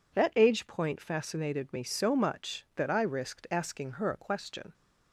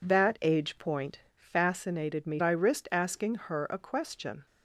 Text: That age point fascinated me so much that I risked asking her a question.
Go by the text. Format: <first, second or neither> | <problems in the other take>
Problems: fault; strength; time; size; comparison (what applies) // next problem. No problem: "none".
first | pauses between "point" and "fascinated"; slight; at 1.2 s; 0.16 s long // skips "so much that"; at 2.4 s